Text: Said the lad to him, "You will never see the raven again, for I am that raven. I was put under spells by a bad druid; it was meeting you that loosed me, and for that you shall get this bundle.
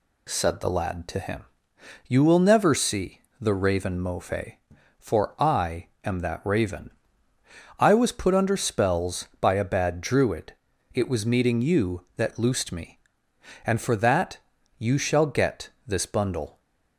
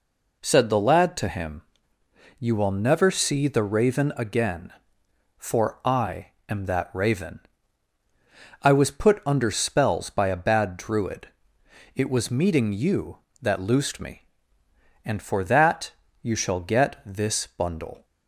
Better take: second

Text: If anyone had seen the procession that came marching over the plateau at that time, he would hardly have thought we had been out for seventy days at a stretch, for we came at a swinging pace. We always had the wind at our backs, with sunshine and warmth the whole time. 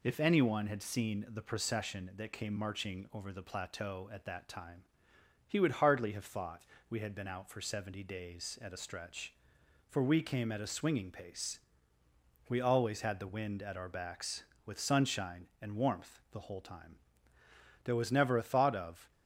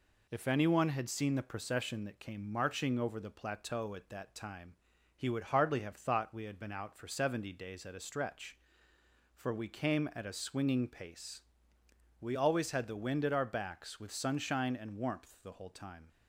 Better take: second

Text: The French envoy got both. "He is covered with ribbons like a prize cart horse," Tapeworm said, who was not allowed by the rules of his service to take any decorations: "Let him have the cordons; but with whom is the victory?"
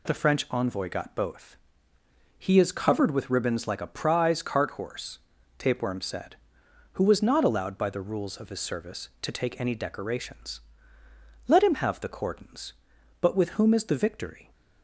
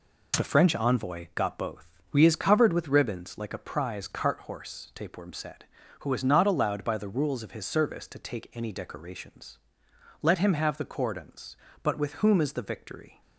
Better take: first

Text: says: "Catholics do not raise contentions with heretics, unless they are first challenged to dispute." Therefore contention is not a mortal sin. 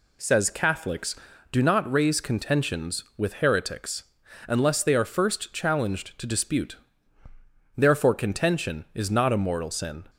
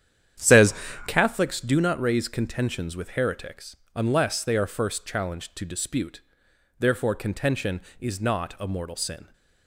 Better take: first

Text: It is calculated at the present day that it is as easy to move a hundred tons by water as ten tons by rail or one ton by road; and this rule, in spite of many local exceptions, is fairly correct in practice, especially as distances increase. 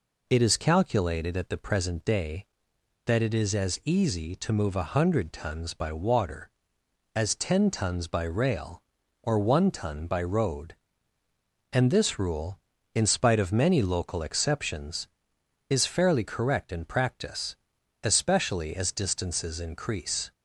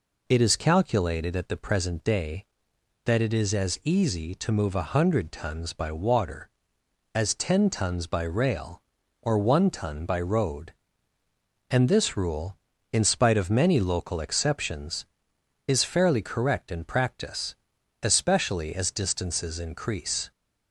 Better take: neither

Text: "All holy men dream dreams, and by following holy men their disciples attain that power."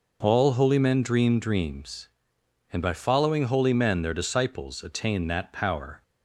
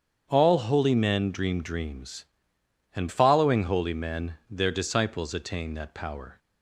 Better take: first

